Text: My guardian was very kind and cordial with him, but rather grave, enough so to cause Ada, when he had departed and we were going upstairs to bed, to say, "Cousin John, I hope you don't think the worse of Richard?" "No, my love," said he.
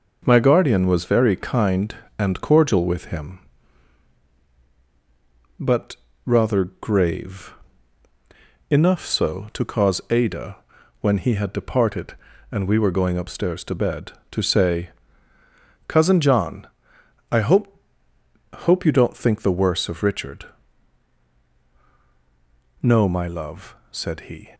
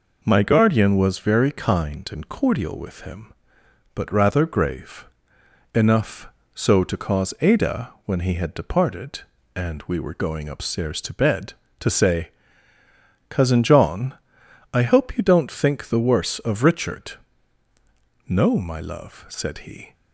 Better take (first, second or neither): second